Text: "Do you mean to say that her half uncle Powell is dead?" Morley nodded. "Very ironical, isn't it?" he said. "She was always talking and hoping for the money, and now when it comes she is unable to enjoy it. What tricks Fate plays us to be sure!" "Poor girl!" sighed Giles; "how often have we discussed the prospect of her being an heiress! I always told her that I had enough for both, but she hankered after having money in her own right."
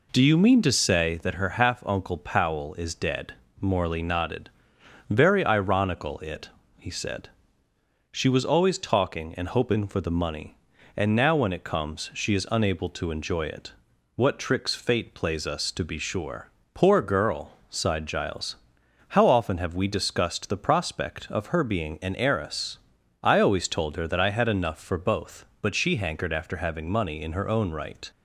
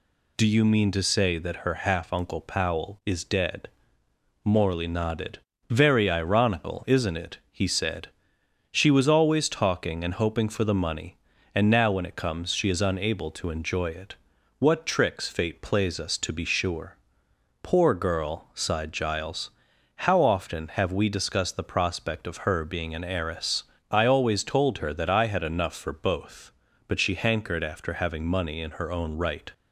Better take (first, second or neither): second